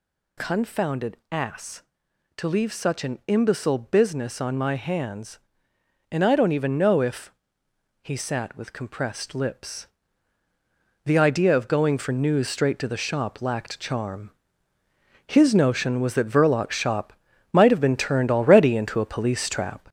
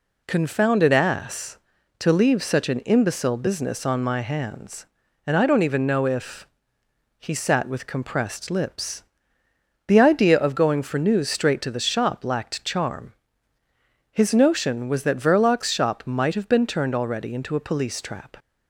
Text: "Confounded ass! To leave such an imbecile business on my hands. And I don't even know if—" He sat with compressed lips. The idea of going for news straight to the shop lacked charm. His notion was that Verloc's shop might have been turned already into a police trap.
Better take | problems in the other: second | gets louder; noticeable; throughout; 4.5 dB // pauses between "Confounded" and "ass"; slight; at 1.1 s; 0.16 s long // pauses between "shop" and "might"; at 17.1 s; 0.38 s long

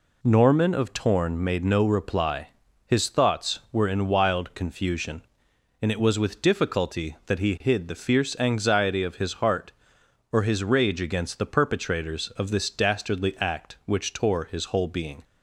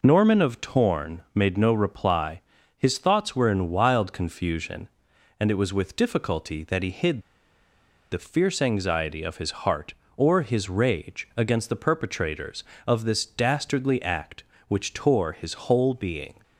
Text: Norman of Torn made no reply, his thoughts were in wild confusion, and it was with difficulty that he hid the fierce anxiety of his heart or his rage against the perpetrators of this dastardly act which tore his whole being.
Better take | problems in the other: first | pauses between "hid" and "the"; noticeable; at 7.2 s; 0.91 s long

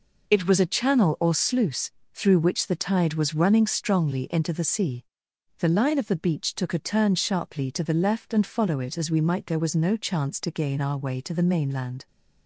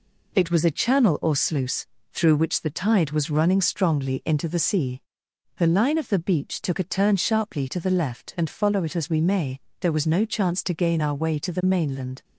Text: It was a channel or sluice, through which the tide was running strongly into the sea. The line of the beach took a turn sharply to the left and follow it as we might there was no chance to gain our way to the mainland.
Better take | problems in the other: first | says "may" for "might"; at 9.1 s

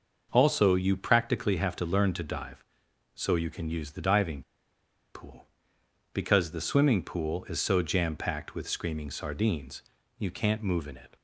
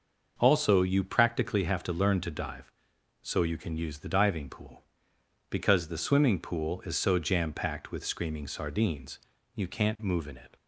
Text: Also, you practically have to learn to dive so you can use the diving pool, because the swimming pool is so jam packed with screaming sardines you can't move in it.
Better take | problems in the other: second | pauses between "diving" and "pool"; noticeable; at 4.4 s; 0.71 s long // pauses between "sardines" and "you"; slight; at 9.8 s; 0.36 s long; slight in the second

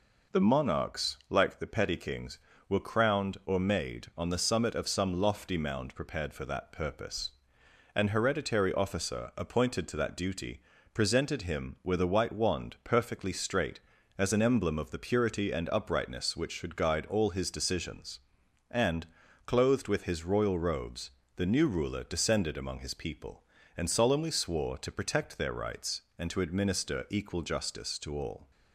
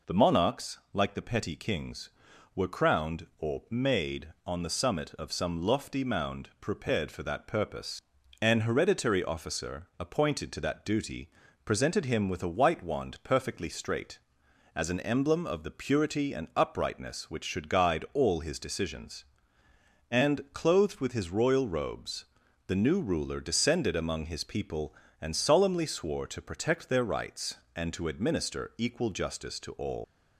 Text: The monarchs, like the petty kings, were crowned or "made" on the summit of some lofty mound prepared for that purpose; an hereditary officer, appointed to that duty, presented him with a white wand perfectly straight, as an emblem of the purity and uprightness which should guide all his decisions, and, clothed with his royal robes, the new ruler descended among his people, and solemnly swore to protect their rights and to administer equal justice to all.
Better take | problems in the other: first | leaves "all" unfinished; at 30.0 s; 140 ms

